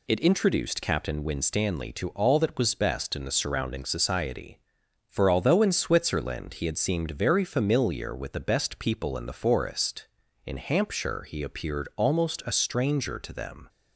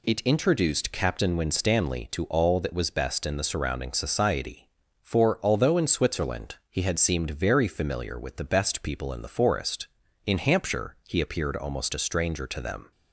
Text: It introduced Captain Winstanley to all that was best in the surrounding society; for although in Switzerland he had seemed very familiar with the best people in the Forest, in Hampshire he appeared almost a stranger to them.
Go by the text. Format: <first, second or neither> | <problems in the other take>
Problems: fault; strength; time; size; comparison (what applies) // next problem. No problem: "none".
neither | none